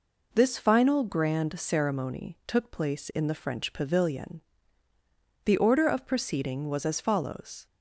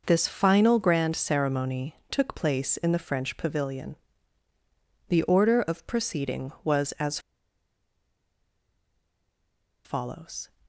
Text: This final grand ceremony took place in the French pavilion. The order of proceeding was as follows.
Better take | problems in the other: first | pauses between "ceremony" and "took"; slight; at 1.9 s; 0.16 s long // pauses between "as" and "follows"; strong; at 7.1 s; 2.6 s long

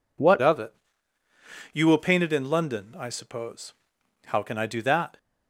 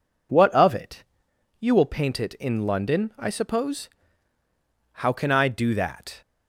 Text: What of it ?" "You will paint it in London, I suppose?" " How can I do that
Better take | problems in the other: second | changes voice at "of"; from 0.4 s on; 4.7 s long

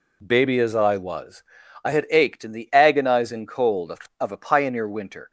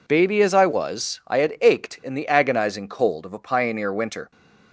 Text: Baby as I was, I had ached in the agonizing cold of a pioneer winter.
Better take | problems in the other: second | says "of" twice; at 4.1 s

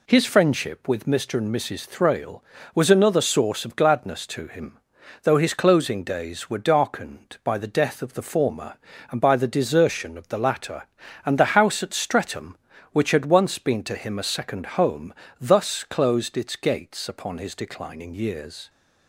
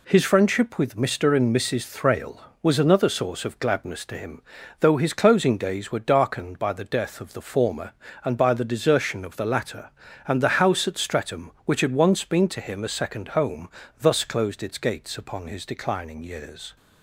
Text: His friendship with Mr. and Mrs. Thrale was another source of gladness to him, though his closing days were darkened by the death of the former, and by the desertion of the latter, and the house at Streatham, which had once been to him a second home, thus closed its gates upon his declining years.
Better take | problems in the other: neither | none

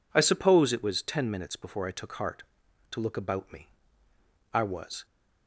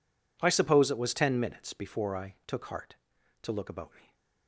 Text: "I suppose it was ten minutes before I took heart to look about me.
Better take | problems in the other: second | goes on to say "I was"; from 4.5 s on; 0.54 s long

